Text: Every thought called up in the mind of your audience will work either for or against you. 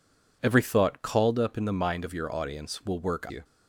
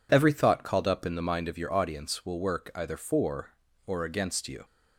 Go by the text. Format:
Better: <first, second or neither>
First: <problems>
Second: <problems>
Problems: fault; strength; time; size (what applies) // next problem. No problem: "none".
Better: second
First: skips "either for or against"; at 3.2 s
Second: none